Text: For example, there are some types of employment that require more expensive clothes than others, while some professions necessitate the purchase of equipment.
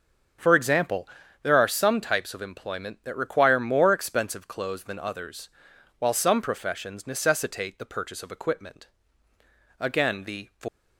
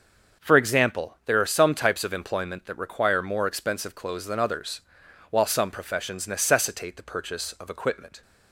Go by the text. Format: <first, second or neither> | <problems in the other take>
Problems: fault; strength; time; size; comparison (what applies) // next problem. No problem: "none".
second | starts louder than the rest; until 1.7 s; 6.5 dB; also in the second // goes on to say "Again the"; noticeable; from 9.7 s on; 0.70 s long